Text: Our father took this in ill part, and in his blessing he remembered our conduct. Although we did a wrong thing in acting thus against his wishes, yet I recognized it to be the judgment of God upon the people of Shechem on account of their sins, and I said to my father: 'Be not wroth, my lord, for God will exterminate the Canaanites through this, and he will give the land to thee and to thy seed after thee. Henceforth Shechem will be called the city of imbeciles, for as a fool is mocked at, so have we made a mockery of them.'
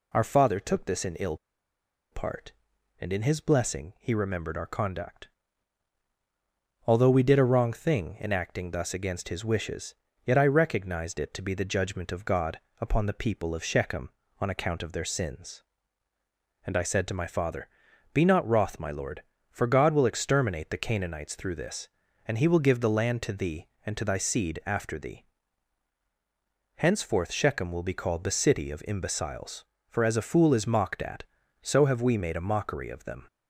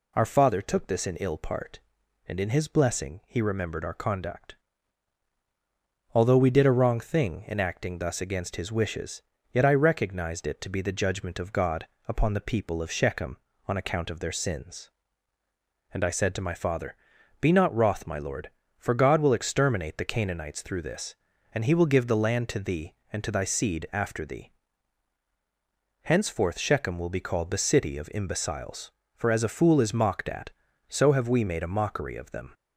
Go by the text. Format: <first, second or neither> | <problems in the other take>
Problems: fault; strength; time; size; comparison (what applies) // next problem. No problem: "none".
second | pauses between "ill" and "part"; noticeable; at 1.3 s; 0.76 s long // pauses between "God" and "upon"; slight; at 12.5 s; 0.20 s long; slight in the second